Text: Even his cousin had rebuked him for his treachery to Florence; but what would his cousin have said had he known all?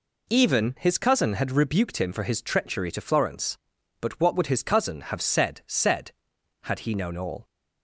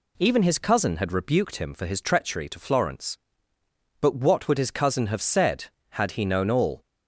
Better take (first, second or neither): second